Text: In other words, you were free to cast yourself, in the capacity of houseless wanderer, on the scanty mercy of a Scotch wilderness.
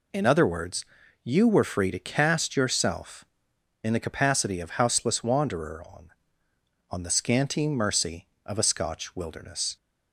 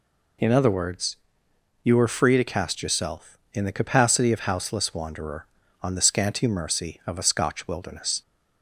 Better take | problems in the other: second | says "on" twice; at 6.8 s

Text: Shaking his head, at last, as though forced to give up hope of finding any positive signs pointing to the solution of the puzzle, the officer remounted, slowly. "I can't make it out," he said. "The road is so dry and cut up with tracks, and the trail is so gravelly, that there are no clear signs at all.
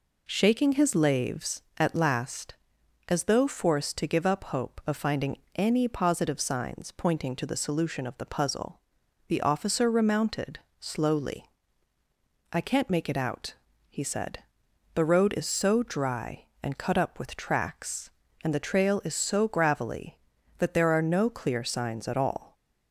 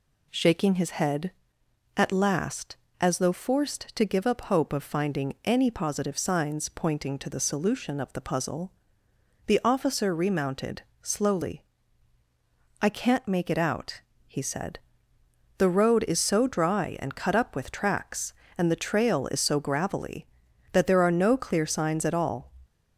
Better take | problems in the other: second | says "laves" for "head"; at 0.9 s // pauses between "finding" and "any"; slight; at 5.3 s; 0.18 s long

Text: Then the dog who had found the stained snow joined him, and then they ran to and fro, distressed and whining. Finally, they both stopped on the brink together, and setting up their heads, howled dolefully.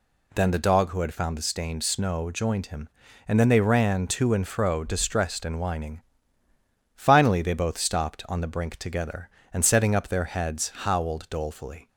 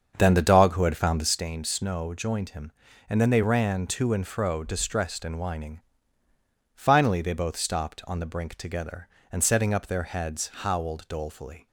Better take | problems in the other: first | starts louder than the rest; until 1.4 s; 7 dB

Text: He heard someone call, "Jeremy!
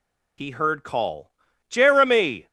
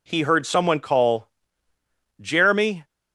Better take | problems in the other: second | skips "someone"; at 0.8 s

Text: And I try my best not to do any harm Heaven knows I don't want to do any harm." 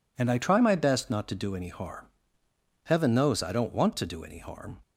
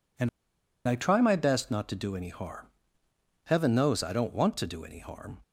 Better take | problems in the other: first | pauses between "And" and "I"; noticeable; at 0.2 s; 0.59 s long // pauses between "harm" and "Heaven"; noticeable; at 2.6 s; 0.78 s long; noticeable in the first

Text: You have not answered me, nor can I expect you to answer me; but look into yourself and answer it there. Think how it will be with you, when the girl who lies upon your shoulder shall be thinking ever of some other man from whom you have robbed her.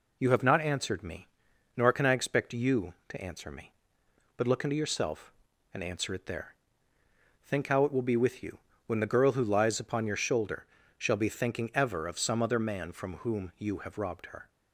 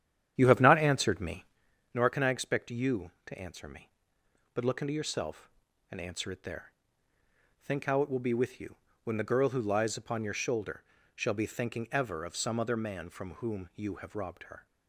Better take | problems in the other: first | starts louder than the rest; strong; until 1.7 s; 10 dB // pauses between "shoulder" and "shall"; slight; at 10.8 s; 0.30 s long; slight in the first

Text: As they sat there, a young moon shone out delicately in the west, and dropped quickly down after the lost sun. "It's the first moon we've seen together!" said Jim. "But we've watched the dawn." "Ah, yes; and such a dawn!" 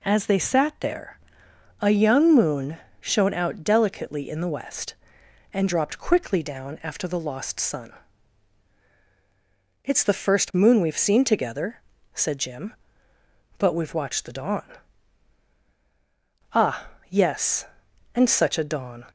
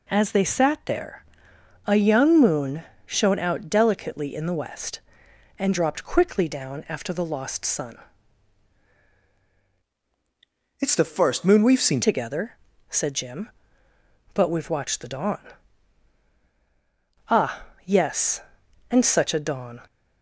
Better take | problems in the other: first | pauses between "moon" and "shone"; slight; at 2.8 s; 0.22 s long; slight in the first // changes voice from "It's" to "seen"; from 10.7 to 12.0 s; 1.3 s long

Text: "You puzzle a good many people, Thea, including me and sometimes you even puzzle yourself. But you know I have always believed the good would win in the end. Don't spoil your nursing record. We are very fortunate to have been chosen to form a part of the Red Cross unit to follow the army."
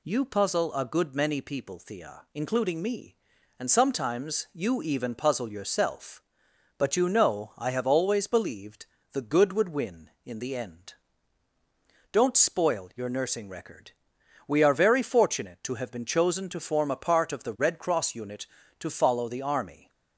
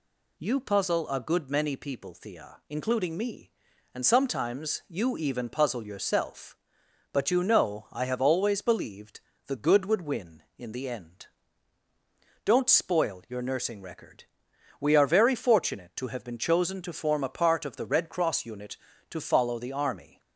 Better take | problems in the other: neither | pauses between "believed" and "the"; slight; the same in both

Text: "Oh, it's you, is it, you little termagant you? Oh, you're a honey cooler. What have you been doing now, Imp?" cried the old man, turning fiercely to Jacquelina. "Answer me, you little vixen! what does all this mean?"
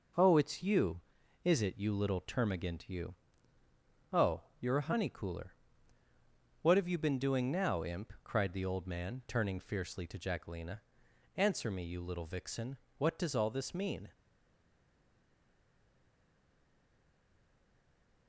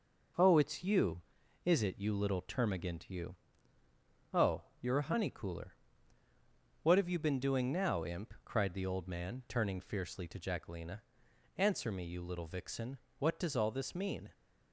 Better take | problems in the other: second | stays silent after the last word; strong; from 14.1 s on; 4.1 s long

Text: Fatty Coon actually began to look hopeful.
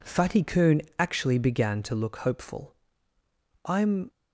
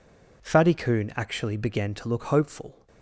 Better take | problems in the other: second | pauses between "Coon" and "actually"; slight; at 0.8 s; 0.16 s long // goes on to say "I'm"; slight; from 3.6 s on; 0.44 s long

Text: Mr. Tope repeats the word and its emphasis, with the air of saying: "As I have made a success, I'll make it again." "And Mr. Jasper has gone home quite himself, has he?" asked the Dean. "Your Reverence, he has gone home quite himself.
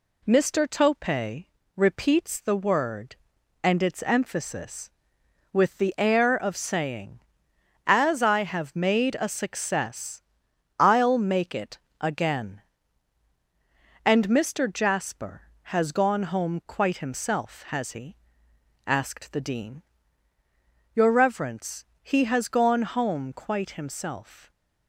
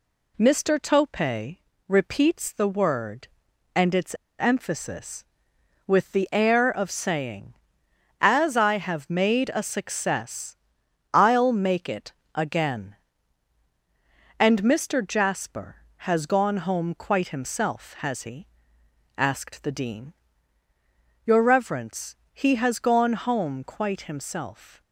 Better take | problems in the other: first | pauses between "Tope" and "repeats"; slight; at 1.5 s; 0.30 s long; slight in the first // pauses between "its" and "emphasis"; slight; at 4.1 s; 0.22 s long // pauses between "it" and "again"; slight; at 12.1 s; 0.20 s long; slight in the first

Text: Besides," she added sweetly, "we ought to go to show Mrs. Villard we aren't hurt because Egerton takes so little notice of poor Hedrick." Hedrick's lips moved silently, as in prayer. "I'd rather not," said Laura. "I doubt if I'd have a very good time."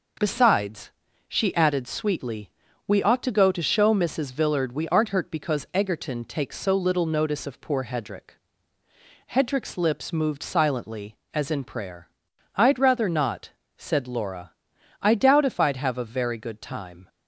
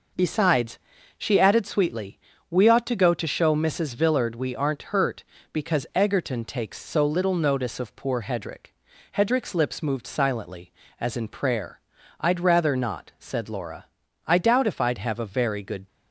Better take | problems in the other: first | stops before "time"; at 15.8 s

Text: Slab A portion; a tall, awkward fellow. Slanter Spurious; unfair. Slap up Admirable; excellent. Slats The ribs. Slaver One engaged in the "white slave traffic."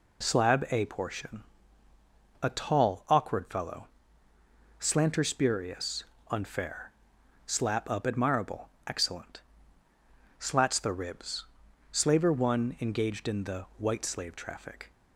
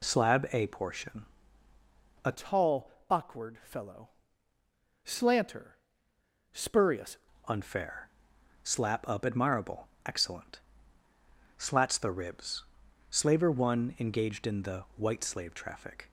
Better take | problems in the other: first | changes voice from "tall" to "Spurious"; from 2.3 to 7.1 s; 4.8 s long // pauses between "Slanter" and "Spurious"; noticeable; at 5.7 s; 0.80 s long

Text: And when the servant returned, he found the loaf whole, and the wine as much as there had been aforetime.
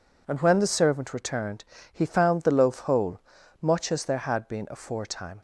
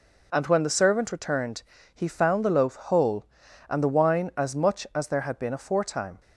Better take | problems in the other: second | skips "and the wine as"; at 3.3 s

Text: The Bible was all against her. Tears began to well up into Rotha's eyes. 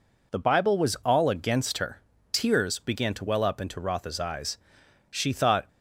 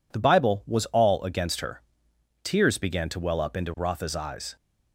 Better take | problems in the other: second | goes on to say "She thought"; from 5.0 s on; 0.58 s long

